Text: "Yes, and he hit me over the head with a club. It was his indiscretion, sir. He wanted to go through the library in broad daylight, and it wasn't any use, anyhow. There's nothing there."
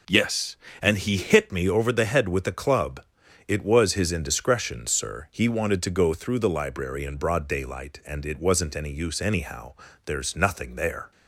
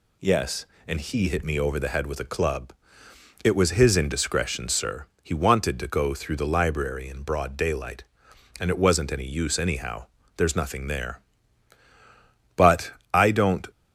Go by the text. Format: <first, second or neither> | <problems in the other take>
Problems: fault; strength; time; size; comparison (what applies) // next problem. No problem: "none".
first | goes on to say "But I don't"; noticeable; from 12.5 s on; 1.1 s long